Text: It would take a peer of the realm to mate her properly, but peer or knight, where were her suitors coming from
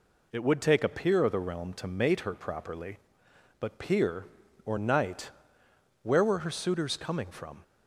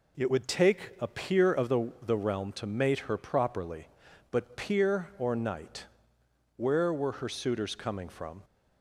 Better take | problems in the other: first | says "the" twice; at 2.0 s

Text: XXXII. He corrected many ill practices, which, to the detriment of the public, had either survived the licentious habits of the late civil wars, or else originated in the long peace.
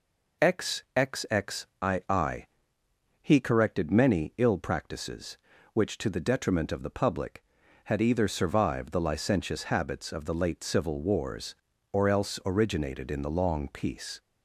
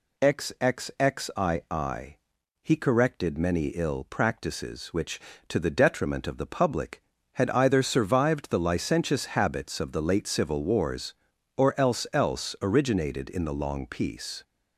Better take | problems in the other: first | says "else" twice; at 12.1 s

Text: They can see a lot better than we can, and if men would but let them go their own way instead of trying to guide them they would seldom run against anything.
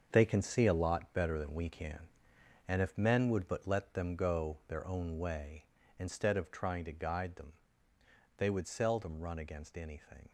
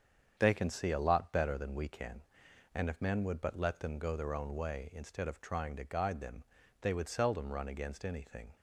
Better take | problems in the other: second | gets quieter; strong; throughout; 10 dB // starts louder than the rest; until 1.1 s; 7 dB; strong in the second // pauses between "them" and "they"; noticeable; at 7.5 s; 0.86 s long; also in the second

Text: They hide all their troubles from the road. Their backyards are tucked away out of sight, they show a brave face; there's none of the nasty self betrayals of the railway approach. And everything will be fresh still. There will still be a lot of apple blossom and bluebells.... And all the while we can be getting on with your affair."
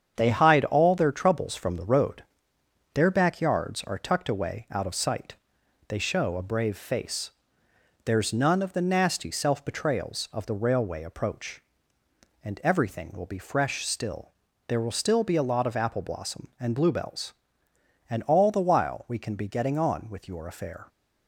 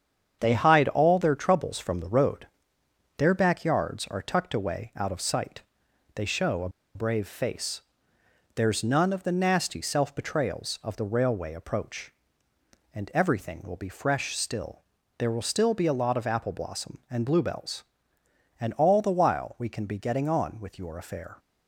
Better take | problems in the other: first | starts louder than the rest; strong; until 1.4 s; 8 dB; strong in the first // pauses between "a" and "brave"; slight; at 6.6 s; 0.26 s long

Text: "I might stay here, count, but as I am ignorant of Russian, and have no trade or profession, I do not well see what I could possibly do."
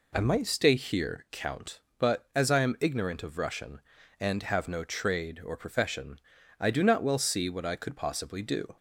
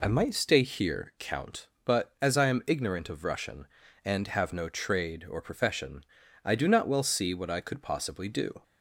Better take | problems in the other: neither | none

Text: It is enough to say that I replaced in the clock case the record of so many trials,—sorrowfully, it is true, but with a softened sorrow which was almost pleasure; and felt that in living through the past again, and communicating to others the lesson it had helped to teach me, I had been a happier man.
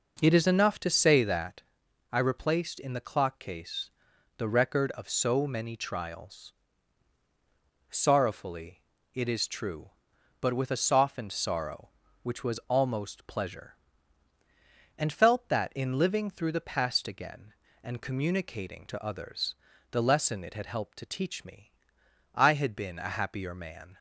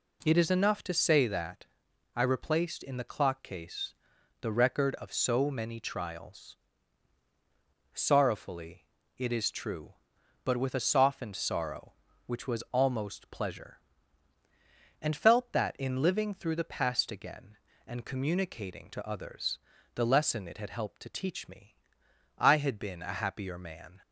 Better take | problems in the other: second | starts louder than the rest; noticeable; until 1.7 s; 5.5 dB // pauses between "that" and "I"; noticeable; at 1.6 s; 0.50 s long; noticeable in the second // pauses between "case" and "the"; noticeable; at 3.9 s; 0.46 s long; noticeable in the second // pauses between "others" and "the"; at 19.5 s; 0.38 s long; also in the second

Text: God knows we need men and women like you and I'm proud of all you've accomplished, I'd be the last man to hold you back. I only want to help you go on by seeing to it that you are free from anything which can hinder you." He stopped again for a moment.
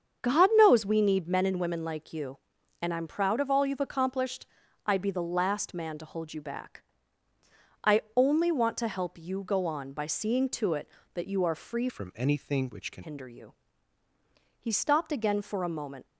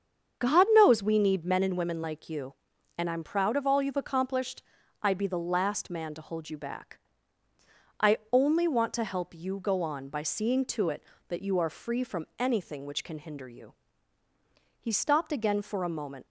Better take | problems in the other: second | starts louder than the rest; strong; until 1.2 s; 7 dB; strong in the second // changes voice from "from" to "can"; from 11.8 to 13.0 s; 1.2 s long

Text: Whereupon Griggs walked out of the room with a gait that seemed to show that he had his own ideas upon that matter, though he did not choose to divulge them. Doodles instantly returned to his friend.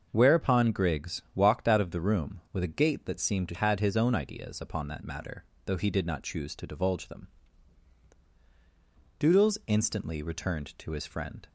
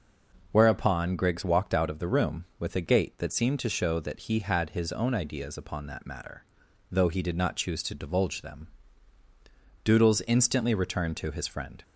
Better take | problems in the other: second | starts louder than the rest; until 1.1 s; 6.5 dB // skips "show that he"; at 3.5 s

